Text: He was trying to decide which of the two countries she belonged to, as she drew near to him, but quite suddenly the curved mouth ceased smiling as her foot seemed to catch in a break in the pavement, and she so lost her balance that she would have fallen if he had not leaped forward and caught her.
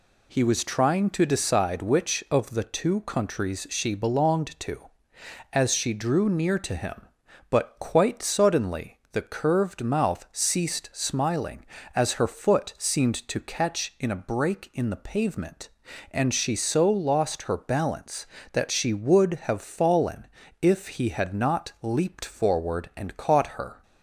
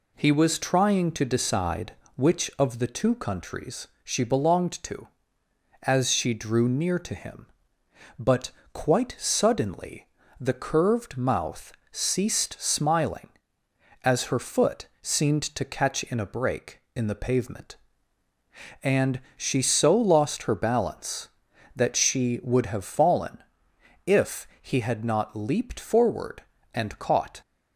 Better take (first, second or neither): first